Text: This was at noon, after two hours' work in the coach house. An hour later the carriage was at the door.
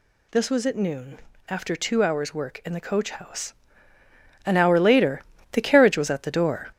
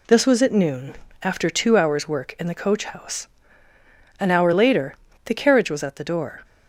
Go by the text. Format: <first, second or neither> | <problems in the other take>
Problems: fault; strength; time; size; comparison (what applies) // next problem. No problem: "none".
second | gets louder; throughout; 6.5 dB // pauses between "later" and "the"; slight; at 5.2 s; 0.30 s long; slight in the second